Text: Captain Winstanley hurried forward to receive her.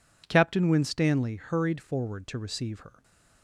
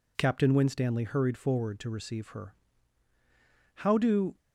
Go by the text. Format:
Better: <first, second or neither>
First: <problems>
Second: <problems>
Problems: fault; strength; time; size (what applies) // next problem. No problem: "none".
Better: first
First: none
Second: goes on to say "How do"; from 3.7 s on; 0.60 s long